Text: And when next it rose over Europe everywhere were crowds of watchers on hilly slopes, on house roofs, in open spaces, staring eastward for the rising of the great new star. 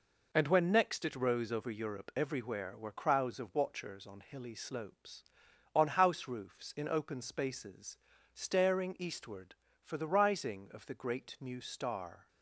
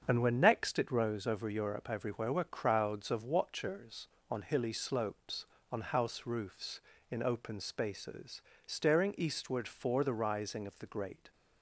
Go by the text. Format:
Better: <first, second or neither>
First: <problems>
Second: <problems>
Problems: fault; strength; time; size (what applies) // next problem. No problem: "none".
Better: first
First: none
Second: starts louder than the rest; until 1.0 s; 7 dB // stops before "new star"; at 11.3 s